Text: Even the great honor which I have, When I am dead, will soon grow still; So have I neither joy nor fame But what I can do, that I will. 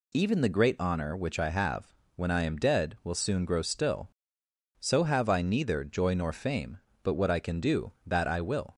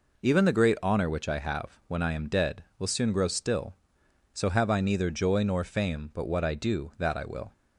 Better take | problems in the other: first | skips "can"; at 6.5 s

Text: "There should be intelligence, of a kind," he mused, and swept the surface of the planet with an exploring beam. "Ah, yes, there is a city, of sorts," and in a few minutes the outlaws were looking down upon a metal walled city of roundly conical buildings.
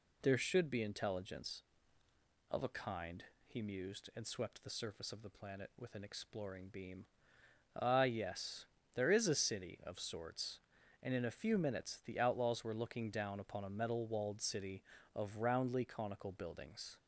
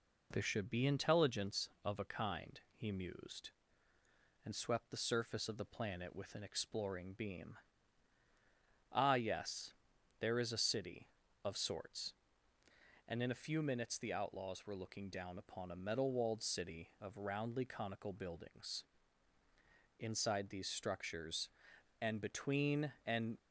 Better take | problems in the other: first | goes on to say "Inside these structures and between and"; strong; from 19.9 s on; 3.4 s long

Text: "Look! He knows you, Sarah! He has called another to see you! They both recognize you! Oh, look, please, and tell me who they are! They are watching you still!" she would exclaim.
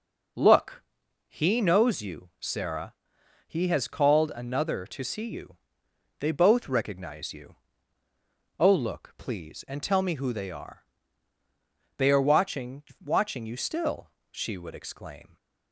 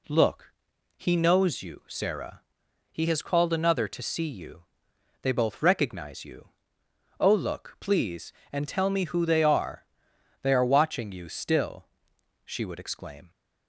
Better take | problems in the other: second | says "watching" twice; at 13.0 s

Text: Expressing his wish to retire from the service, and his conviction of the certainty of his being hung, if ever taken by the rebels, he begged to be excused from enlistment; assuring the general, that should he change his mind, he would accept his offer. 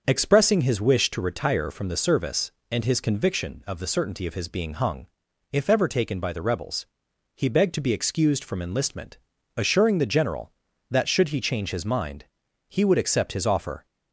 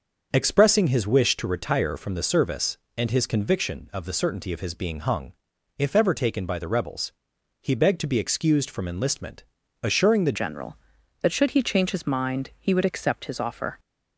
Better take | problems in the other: first | starts louder than the rest; until 1.3 s; 6.5 dB; also in the first // changes voice at "general"; from 10.3 s on; 3.4 s long

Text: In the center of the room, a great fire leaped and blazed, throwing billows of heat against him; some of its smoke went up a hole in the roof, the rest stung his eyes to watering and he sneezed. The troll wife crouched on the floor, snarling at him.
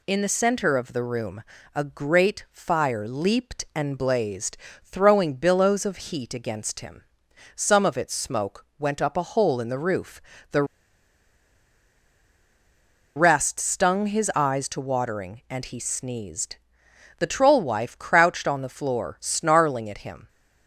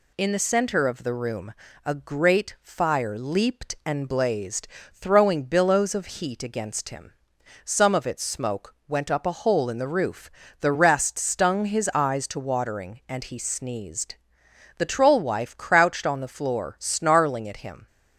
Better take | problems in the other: second | pauses between "the" and "rest"; strong; at 10.6 s; 2.5 s long

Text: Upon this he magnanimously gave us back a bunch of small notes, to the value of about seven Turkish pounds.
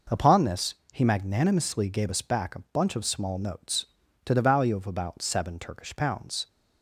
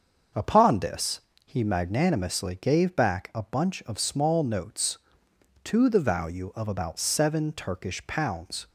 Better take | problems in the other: first | starts louder than the rest; until 1.6 s; 6.5 dB // pauses between "this" and "he"; slight; at 1.1 s; 0.26 s long; slight in the first // skips "us"; at 2.9 s

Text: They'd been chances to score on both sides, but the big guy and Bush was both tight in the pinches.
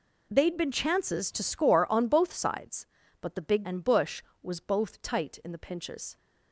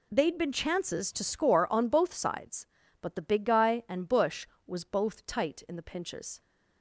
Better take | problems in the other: second | skips "guy"; at 3.6 s

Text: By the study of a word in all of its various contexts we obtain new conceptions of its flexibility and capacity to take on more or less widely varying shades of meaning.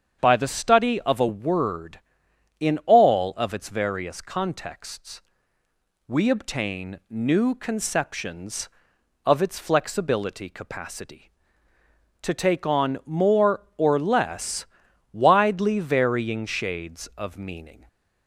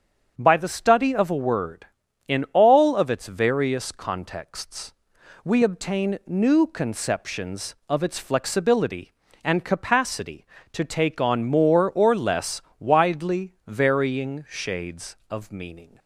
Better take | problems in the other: second | starts louder than the rest; strong; until 1.2 s; 7.5 dB; strong in the second // pauses between "contexts" and "we"; noticeable; at 5.2 s; 0.86 s long; noticeable in the second // skips "and"; at 10.4 s // pauses between "less" and "widely"; noticeable; at 14.6 s; 0.48 s long; slight in the second

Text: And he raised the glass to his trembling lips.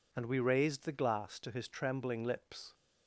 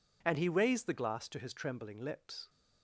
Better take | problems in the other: second | says "we" for "he"; at 0.2 s

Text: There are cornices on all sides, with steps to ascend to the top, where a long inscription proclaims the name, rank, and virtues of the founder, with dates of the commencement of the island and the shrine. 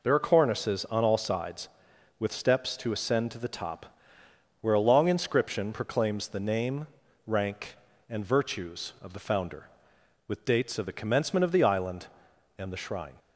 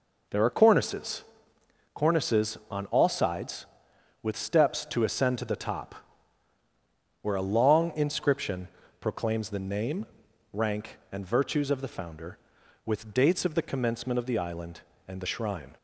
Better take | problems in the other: first | says "cornices" twice; at 1.9 s // pauses between "inscription" and "proclaims"; slight; at 8.6 s; 0.32 s long

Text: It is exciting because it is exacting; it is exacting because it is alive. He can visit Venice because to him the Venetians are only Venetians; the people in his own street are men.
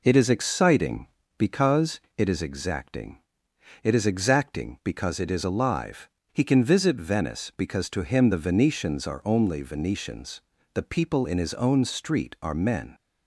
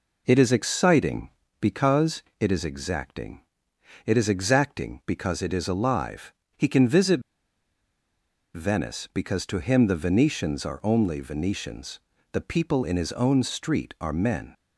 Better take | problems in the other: first | pauses between "because" and "it"; slight; at 2.2 s; 0.18 s long; slight in the first // pauses between "visit" and "Venice"; strong; at 7.2 s; 1.3 s long

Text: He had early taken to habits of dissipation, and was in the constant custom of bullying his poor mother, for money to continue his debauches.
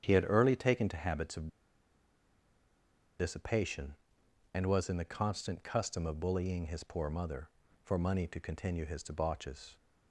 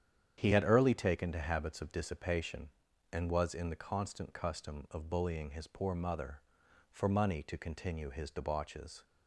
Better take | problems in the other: second | starts louder than the rest; strong; until 1.0 s; 9 dB; strong in the second // pauses between "of" and "dissipation"; strong; at 1.4 s; 1.7 s long

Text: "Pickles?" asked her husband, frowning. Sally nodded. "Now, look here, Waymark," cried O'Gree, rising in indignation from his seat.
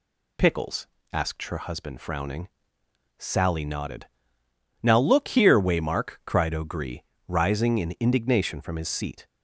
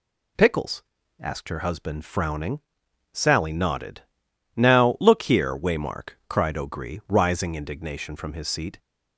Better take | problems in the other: first | skips "in"; at 7.5 s

